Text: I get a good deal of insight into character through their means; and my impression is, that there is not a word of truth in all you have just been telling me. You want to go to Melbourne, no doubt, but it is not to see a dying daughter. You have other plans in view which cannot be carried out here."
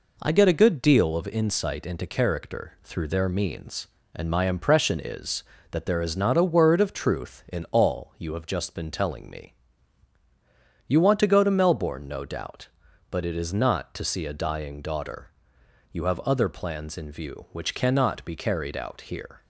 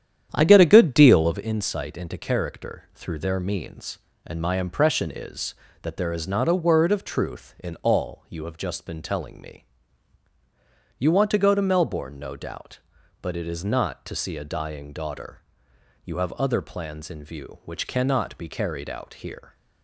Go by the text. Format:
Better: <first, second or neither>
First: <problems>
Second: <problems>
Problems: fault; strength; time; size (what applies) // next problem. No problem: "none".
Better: first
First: none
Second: starts louder than the rest; strong; until 1.4 s; 9.5 dB